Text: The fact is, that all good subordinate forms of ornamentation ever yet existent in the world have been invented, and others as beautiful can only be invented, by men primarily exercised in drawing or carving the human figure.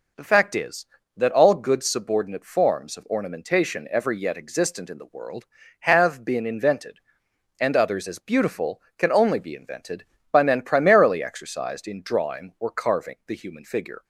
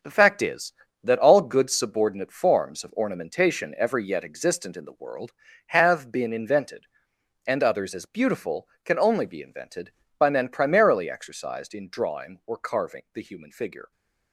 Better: first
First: none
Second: gets quieter; strong; throughout; 8 dB

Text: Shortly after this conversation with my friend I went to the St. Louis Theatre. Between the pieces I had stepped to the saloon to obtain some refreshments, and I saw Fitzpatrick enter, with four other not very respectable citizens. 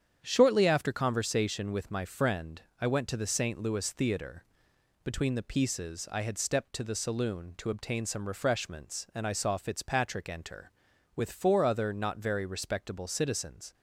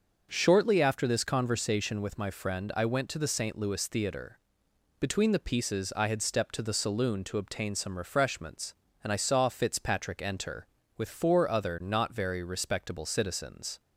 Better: second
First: starts louder than the rest; strong; until 1.2 s; 8.5 dB // skips "this"; at 0.9 s // pauses between "friend" and "I"; slight; at 2.6 s; 0.18 s long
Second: starts louder than the rest; noticeable; until 1.3 s; 6 dB

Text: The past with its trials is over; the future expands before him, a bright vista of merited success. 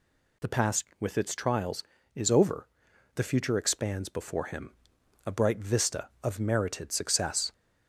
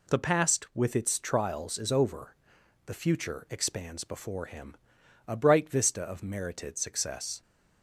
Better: neither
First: none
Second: none

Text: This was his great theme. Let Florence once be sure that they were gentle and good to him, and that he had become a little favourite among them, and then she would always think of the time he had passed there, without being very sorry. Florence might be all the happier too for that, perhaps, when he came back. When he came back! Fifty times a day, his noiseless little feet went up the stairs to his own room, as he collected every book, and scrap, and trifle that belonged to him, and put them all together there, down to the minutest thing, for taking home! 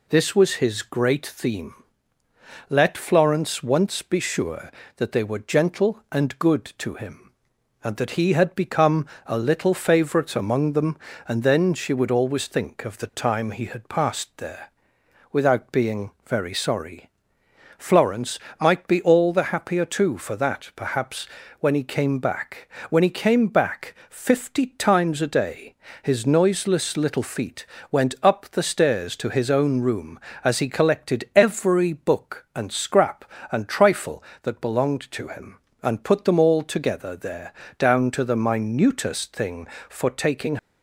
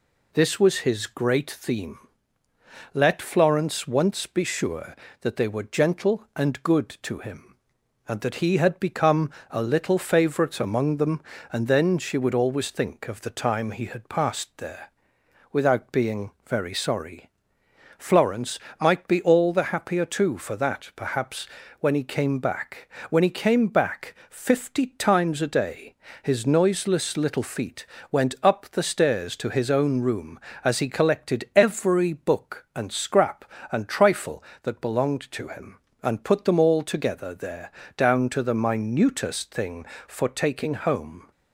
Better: second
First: pauses between "become" and "a"; slight; at 9.0 s; 0.18 s long // pauses between "Florence" and "might"; slight; at 18.4 s; 0.20 s long // pauses between "feet" and "went"; slight; at 27.6 s; 0.28 s long // stops before "home"; at 40.5 s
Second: pauses between "become" and "a"; slight; at 9.3 s; 0.18 s long // pauses between "Florence" and "might"; slight; at 18.6 s; 0.20 s long // pauses between "feet" and "went"; slight; at 27.8 s; 0.28 s long

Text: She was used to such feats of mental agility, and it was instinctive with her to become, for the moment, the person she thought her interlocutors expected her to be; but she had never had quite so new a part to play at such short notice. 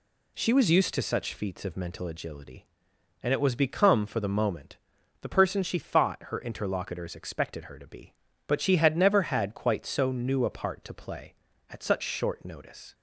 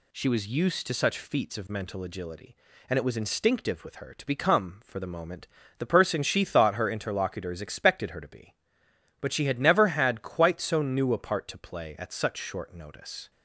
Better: second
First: skips "instinctive with her to"; at 3.5 s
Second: none

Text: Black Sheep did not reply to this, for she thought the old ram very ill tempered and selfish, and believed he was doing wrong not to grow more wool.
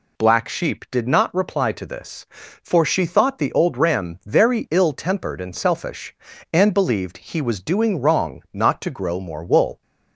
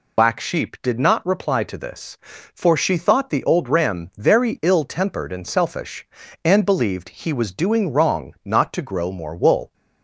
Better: first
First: none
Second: loses the start of "Black"; at 0.1 s; 90 ms

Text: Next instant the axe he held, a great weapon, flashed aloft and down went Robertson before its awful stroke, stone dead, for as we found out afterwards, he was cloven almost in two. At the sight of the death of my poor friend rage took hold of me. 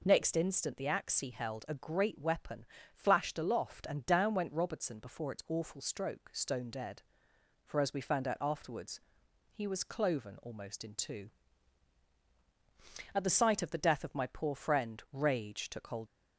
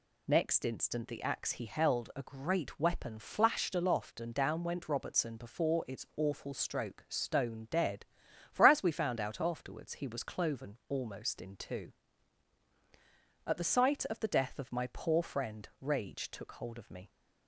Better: second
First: stops before "of me"; at 16.0 s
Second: none

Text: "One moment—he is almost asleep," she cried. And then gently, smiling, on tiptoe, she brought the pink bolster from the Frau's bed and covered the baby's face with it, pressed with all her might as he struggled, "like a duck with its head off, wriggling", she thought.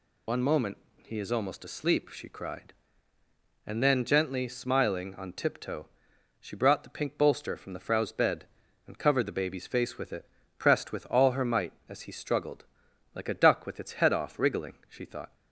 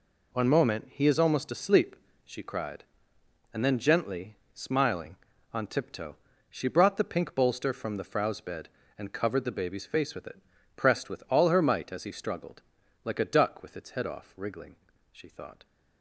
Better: second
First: loses the start of "One"; at 0.2 s; 70 ms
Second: none

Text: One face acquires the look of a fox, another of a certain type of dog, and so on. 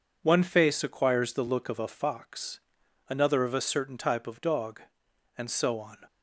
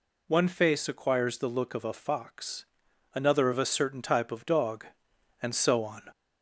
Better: first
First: none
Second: gets louder; slight; throughout; 2.5 dB

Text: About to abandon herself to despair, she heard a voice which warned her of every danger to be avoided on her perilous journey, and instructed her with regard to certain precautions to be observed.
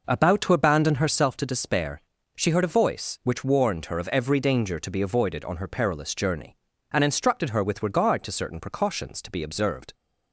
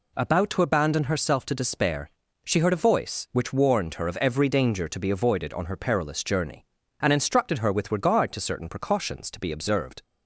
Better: second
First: starts louder than the rest; noticeable; until 1.3 s; 5 dB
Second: none

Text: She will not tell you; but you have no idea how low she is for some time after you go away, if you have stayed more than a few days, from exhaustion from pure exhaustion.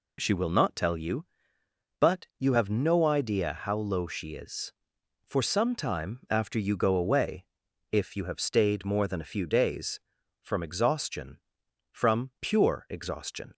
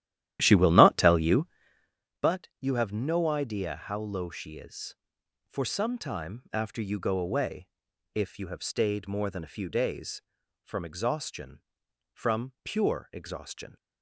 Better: first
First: none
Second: starts louder than the rest; strong; until 2.0 s; 12.5 dB

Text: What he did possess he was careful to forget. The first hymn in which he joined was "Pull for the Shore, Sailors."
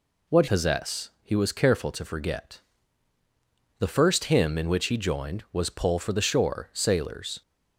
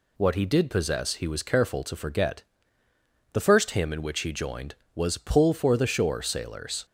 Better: second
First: skips "he did"; at 0.4 s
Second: none

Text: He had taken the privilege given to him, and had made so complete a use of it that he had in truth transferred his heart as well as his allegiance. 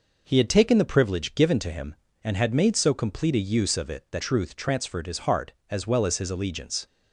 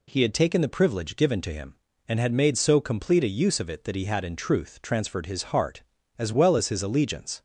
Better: second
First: skips "he had in"; at 4.2 s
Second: none

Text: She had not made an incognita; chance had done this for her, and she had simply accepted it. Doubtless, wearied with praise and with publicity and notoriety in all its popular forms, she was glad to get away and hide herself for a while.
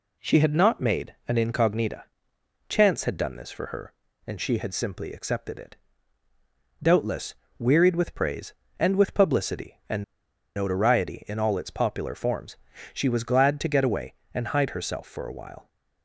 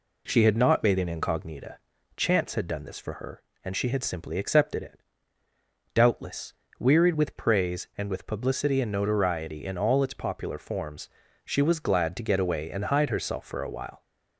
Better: second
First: pauses between "and" and "notoriety"; noticeable; at 10.0 s; 0.53 s long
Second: none

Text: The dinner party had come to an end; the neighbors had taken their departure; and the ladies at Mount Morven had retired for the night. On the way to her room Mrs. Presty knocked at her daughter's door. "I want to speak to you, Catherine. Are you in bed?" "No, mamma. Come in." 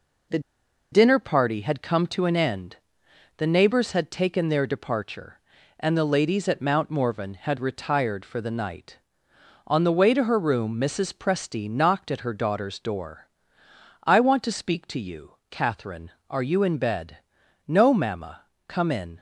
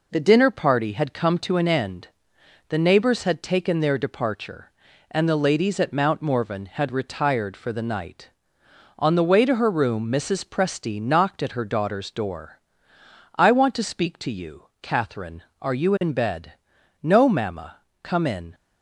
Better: second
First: pauses between "The" and "dinner"; noticeable; at 0.3 s; 0.52 s long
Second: none

